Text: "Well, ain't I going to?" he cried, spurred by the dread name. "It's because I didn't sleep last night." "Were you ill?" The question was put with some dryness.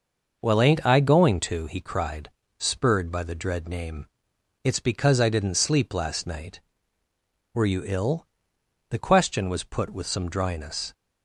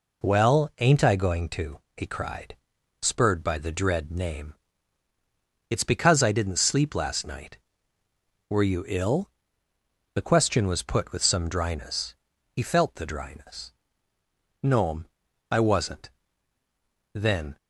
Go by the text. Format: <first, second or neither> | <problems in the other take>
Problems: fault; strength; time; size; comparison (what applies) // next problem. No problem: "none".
first | goes on to say "He felt the dryness No'm I wasn't Then"; strong; from 12.5 s on; 5.0 s long